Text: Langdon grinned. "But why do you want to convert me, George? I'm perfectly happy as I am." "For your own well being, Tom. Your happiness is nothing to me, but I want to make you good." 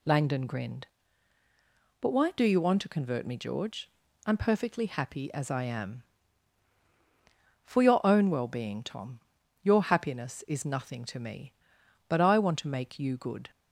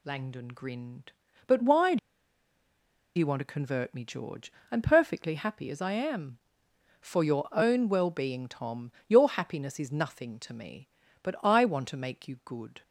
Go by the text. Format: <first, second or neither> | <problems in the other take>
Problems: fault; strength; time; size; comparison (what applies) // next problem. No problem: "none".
first | pauses between "do" and "you"; at 1.9 s; 1.1 s long